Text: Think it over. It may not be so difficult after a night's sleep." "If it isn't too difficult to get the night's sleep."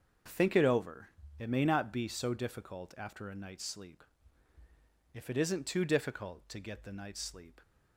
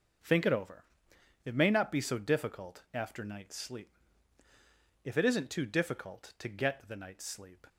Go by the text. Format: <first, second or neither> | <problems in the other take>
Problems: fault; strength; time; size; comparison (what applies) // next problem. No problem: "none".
first | starts louder than the rest; noticeable; until 1.8 s; 6 dB; also in the first // skips "a"; at 3.2 s